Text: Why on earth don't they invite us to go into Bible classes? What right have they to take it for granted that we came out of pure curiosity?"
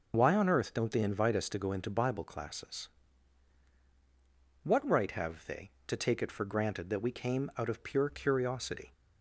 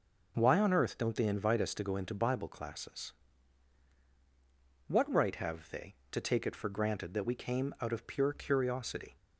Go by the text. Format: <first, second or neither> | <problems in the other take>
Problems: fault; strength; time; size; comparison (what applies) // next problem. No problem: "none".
second | loses the start of "Why"; at 0.1 s; 25 ms